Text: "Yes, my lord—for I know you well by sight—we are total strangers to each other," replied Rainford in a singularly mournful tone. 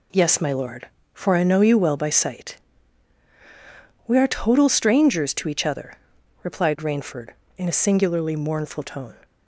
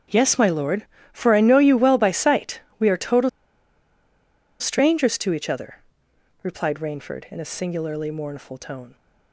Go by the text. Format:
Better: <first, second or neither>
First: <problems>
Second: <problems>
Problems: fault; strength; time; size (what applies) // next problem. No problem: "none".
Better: first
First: none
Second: starts louder than the rest; strong; until 1.3 s; 8 dB // pauses between "total" and "strangers"; strong; at 3.2 s; 1.3 s long